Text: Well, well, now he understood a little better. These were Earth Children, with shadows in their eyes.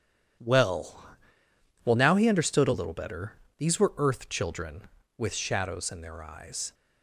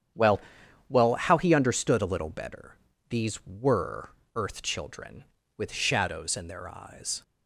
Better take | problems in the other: first | starts louder than the rest; strong; until 1.6 s; 9 dB; strong in the first // says "how" for "now"; at 1.1 s // pauses between "were" and "Earth"; slight; at 4.1 s; 0.24 s long

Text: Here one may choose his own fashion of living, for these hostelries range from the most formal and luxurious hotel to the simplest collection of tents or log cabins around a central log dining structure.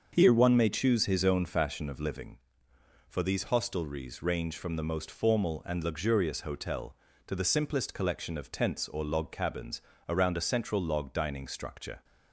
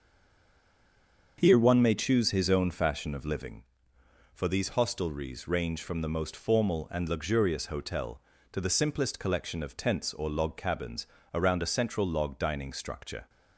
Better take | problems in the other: first | stays silent before the first word; noticeable; until 1.3 s; 1.3 s long // starts louder than the rest; until 2.3 s; 7 dB; also in the first // pauses between "cabins" and "around"; slight; at 11.0 s; 0.26 s long; slight in the first

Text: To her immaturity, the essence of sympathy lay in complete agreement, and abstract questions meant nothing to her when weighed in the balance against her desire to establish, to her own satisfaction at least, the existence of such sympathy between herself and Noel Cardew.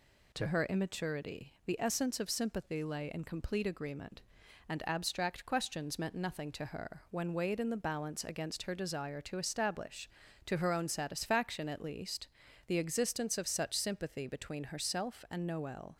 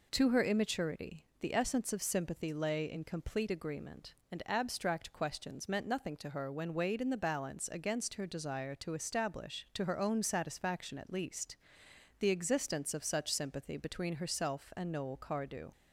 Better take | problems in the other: second | stops before "Cardew"; at 15.9 s

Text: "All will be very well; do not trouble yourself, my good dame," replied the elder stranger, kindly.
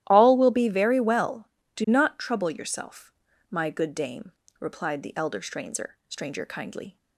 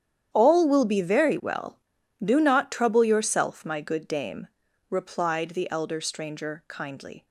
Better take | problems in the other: second | starts louder than the rest; strong; until 1.0 s; 13 dB; strong in the second // says "stranger" twice; at 6.0 s

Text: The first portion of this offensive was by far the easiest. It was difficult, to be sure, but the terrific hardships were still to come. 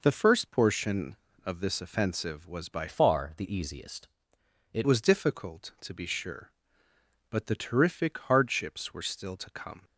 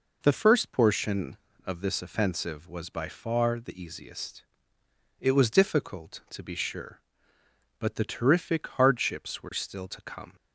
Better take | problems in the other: second | changes voice from "far" to "It"; from 2.8 to 4.8 s; 2.0 s long

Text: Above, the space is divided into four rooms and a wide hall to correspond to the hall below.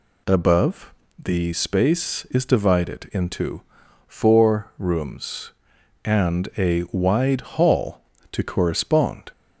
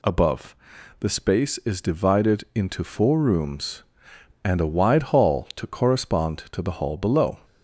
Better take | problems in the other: second | pauses between "into" and "four"; at 3.6 s; 0.44 s long // stops before "to the hall below"; at 9.3 s

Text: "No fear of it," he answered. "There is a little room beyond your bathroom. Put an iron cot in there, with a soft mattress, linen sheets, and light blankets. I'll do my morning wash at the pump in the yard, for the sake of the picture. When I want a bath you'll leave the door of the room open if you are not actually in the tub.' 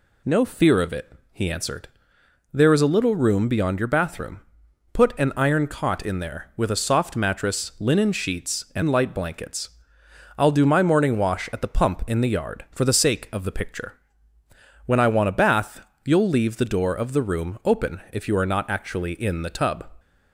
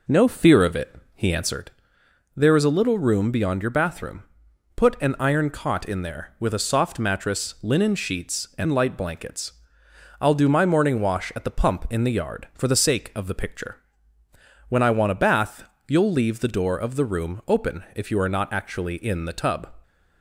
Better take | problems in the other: first | starts louder than the rest; noticeable; until 1.6 s; 5 dB // pauses between "bath" and "you'll"; slight; at 15.6 s; 0.20 s long; slight in the first

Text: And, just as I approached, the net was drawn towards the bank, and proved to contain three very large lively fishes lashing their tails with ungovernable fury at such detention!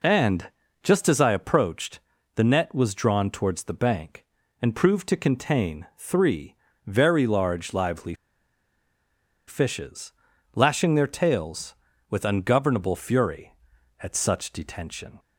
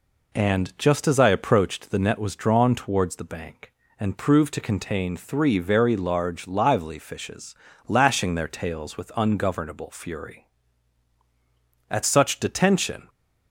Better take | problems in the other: second | pauses between "three" and "very"; slight; at 6.5 s; 0.30 s long // pauses between "lively" and "fishes"; strong; at 8.1 s; 1.3 s long // pauses between "fishes" and "lashing"; at 10.1 s; 0.44 s long; slight in the second

